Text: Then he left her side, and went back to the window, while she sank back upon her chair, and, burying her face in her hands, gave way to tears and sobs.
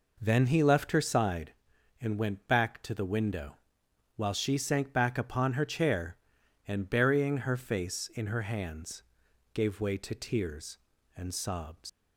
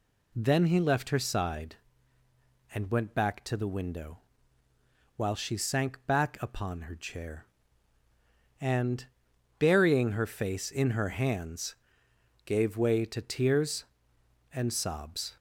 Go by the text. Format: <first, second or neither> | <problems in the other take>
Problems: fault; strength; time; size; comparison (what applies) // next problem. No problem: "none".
second | leaves "sobs" unfinished; at 11.8 s; 90 ms